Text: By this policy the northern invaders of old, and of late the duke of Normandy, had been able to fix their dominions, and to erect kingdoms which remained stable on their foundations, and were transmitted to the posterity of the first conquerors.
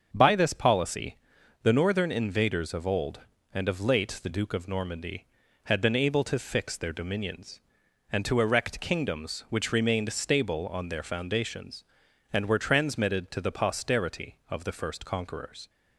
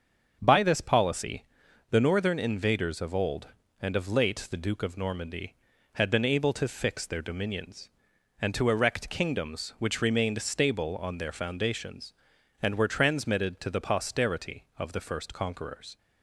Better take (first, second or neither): neither